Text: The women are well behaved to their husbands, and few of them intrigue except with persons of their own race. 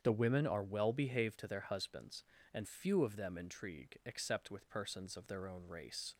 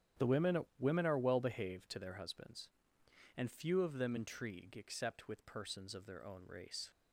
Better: first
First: starts louder than the rest; strong; until 1.0 s; 8 dB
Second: starts louder than the rest; strong; until 1.3 s; 10 dB // says "women" twice; at 0.7 s

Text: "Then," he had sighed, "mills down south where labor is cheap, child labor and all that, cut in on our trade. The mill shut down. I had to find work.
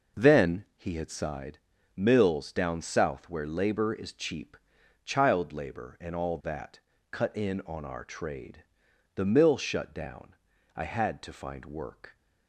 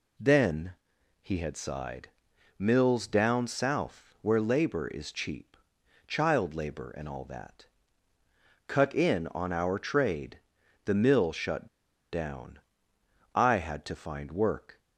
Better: first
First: none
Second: pauses between "shut" and "down"; at 11.6 s; 0.45 s long

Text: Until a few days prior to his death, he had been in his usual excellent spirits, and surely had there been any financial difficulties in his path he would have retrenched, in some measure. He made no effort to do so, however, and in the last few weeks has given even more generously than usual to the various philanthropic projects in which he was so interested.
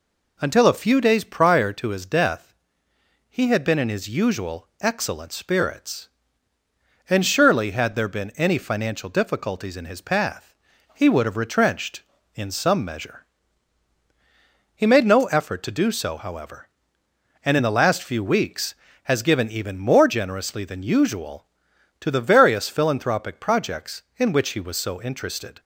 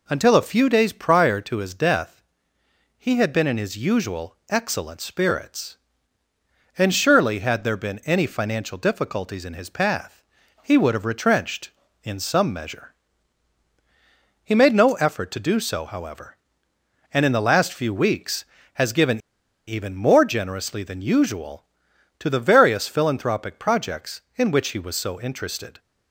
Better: first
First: pauses between "path" and "he"; at 10.5 s; 0.40 s long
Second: pauses between "path" and "he"; at 10.2 s; 0.40 s long // pauses between "given" and "even"; noticeable; at 19.1 s; 0.47 s long

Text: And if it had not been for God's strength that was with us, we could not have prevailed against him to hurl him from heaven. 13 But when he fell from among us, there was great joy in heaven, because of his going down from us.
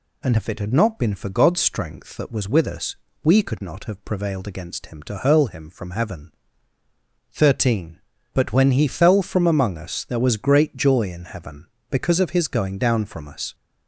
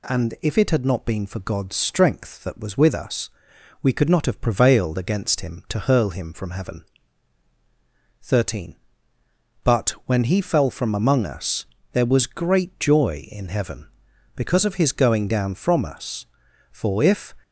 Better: first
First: none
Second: pauses between "But" and "when"; slight; at 9.8 s; 0.16 s long // goes on to say "For if"; noticeable; from 16.7 s on; 0.62 s long

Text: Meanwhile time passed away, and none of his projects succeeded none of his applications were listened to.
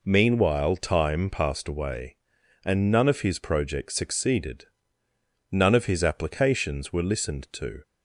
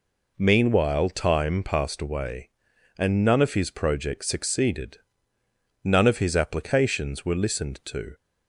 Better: neither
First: pauses between "succeeded" and "none"; noticeable; at 4.6 s; 0.88 s long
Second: pauses between "succeeded" and "none"; noticeable; at 4.9 s; 0.88 s long

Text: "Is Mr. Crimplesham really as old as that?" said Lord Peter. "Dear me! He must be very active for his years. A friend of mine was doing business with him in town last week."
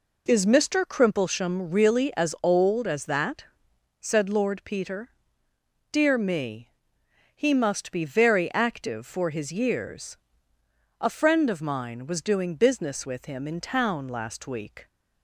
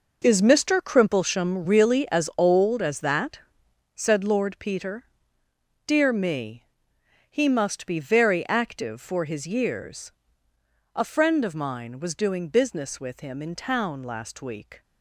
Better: first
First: none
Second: gets quieter; strong; throughout; 12.5 dB

